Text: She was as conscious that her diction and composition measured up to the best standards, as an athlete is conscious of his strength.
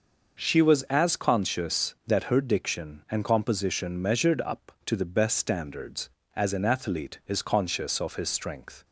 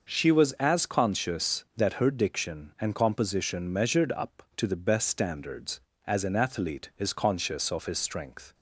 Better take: neither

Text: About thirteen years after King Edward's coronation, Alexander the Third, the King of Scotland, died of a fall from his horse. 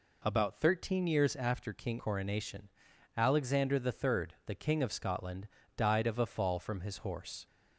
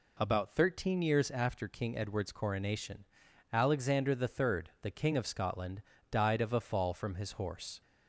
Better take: second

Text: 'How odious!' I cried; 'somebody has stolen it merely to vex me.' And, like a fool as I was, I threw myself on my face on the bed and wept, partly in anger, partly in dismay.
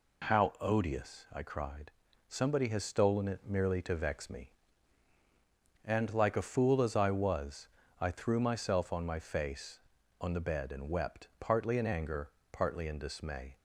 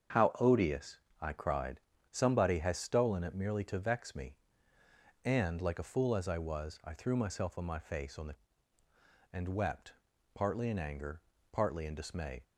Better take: first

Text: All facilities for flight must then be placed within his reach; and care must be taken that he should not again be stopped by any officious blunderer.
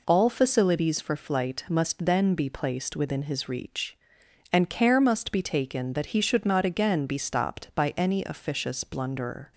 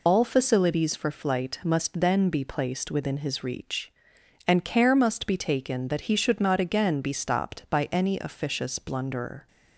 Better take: first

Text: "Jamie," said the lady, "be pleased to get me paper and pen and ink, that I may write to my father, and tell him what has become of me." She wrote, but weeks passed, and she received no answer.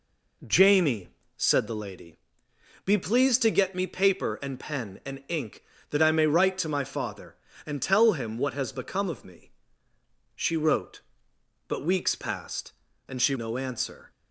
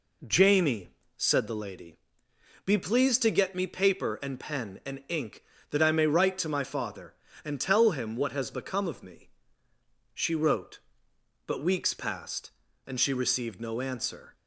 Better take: second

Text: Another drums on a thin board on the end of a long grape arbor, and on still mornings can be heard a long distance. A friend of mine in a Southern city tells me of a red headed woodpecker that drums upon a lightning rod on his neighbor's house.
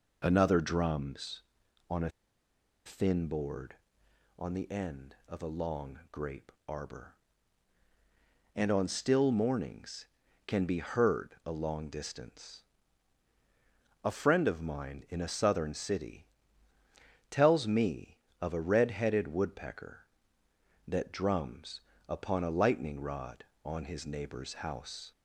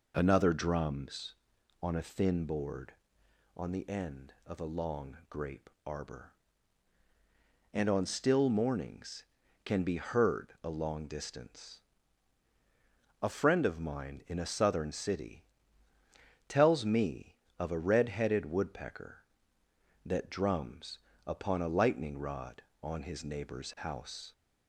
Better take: second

